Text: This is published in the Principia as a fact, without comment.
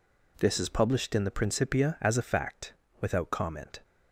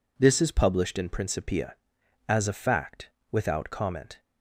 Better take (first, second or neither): first